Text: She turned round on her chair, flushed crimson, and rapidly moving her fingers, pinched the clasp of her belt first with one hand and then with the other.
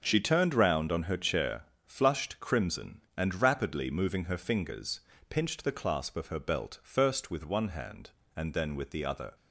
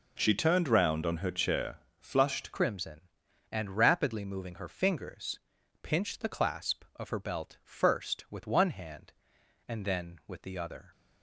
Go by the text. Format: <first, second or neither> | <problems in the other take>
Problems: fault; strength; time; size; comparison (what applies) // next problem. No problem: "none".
first | changes voice at "crimson"; from 2.5 s on; 8.4 s long